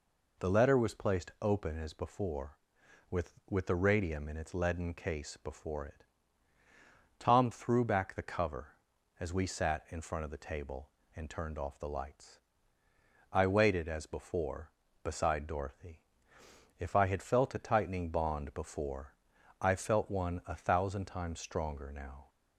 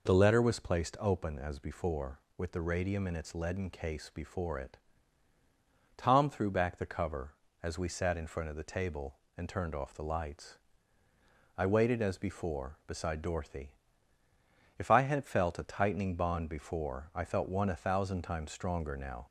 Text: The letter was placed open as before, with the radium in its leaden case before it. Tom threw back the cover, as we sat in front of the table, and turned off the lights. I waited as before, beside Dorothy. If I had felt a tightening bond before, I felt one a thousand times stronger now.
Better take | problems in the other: second | says "with" twice; at 3.4 s

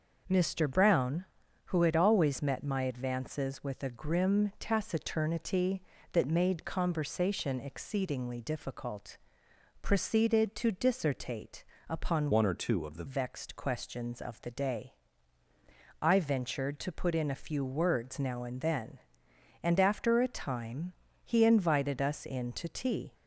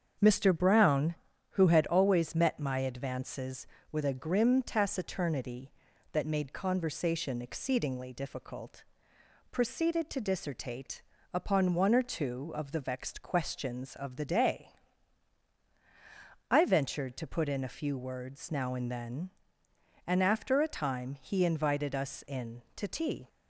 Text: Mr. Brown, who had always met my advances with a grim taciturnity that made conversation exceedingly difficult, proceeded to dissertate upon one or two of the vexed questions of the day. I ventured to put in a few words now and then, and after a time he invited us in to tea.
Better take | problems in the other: second | starts louder than the rest; noticeable; until 1.7 s; 6 dB; strong in the second // pauses between "dissertate" and "upon"; slight; at 11.6 s; 0.24 s long; slight in the second // changes voice from "one" to "the"; from 12.3 to 13.0 s; 0.7 s long // pauses between "time" and "he"; slight; at 20.9 s; 0.32 s long

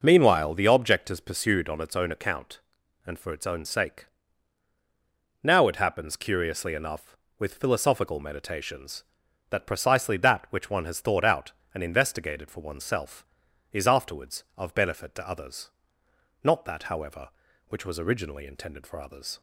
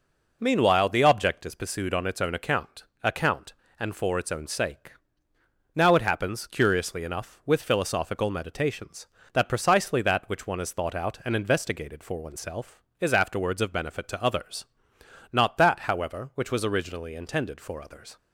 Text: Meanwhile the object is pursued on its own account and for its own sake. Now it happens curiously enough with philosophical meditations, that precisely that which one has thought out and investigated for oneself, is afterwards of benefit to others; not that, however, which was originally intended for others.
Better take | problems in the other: first | says "account" twice; at 3.0 s

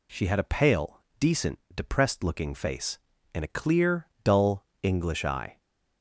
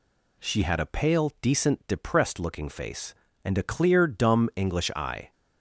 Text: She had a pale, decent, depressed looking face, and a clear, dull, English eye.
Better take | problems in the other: first | says "dumb" for "dull"; at 4.0 s

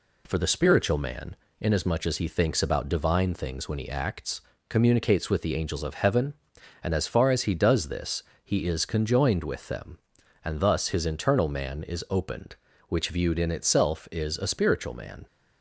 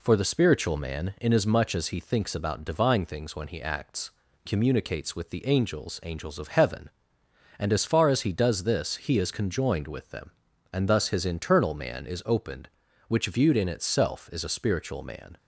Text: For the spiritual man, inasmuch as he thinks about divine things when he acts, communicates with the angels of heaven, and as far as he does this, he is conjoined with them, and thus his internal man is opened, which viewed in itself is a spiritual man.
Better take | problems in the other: first | says "angels" twice; at 6.0 s

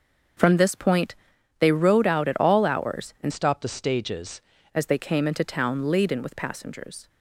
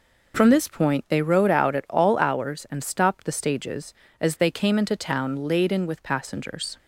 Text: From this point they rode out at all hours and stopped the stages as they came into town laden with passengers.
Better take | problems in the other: second | starts louder than the rest; until 1.8 s; 6.5 dB // pauses between "point" and "they"; at 1.1 s; 0.42 s long // changes voice from "stopped" to "stages"; from 3.3 to 4.4 s; 1.1 s long

